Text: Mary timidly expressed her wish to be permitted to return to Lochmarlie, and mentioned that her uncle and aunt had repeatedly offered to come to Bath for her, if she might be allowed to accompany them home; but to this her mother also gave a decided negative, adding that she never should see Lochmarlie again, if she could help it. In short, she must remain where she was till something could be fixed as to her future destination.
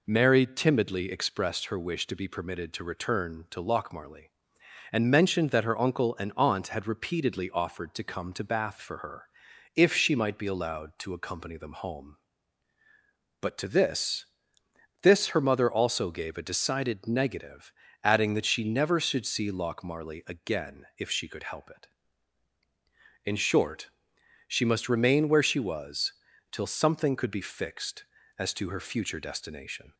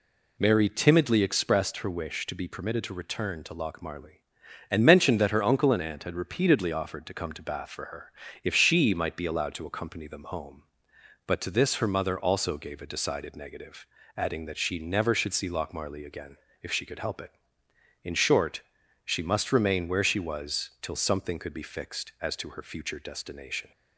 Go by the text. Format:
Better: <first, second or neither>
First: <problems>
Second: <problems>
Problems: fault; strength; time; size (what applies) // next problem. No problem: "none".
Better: second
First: says "this" twice; at 15.0 s // pauses between "was" and "till"; slight; at 26.1 s; 0.36 s long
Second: none